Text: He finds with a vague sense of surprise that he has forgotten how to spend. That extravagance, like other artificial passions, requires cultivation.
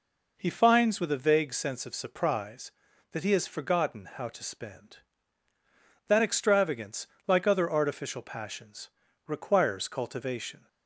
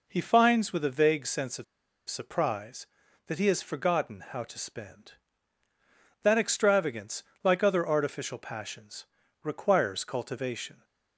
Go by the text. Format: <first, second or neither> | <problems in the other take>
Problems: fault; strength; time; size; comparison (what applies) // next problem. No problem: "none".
first | pauses between "of" and "surprise"; at 1.6 s; 0.44 s long